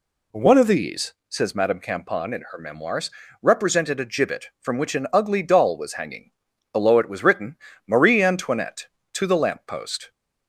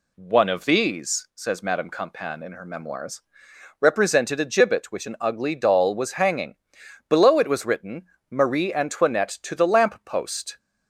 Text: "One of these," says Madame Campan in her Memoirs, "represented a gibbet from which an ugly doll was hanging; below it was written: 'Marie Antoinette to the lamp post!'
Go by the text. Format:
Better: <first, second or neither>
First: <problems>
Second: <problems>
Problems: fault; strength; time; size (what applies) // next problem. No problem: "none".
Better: first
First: none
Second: skips "from"; at 4.9 s